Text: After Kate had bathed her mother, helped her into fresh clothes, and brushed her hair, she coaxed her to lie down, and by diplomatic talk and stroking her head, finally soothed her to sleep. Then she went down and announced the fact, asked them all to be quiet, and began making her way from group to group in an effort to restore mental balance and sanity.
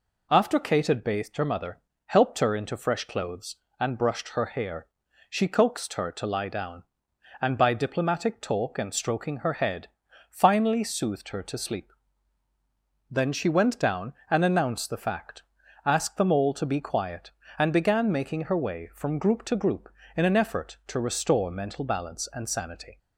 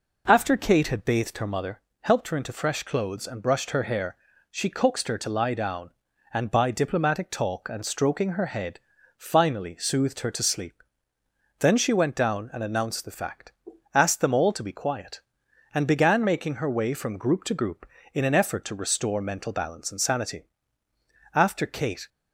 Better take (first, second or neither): first